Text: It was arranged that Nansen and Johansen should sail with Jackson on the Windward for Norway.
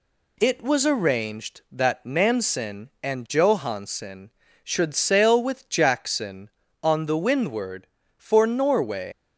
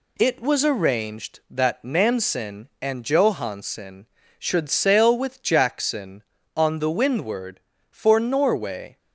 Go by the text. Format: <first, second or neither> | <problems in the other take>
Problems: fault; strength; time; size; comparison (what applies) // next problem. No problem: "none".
second | leaves "Norway" unfinished; at 9.1 s; 120 ms